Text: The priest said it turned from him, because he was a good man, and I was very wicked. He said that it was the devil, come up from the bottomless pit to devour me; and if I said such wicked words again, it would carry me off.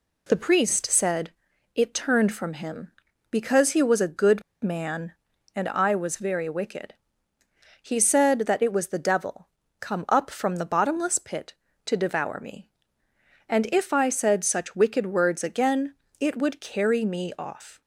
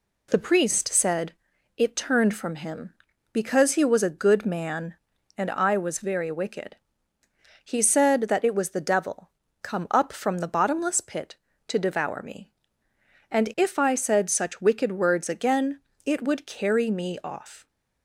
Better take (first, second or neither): second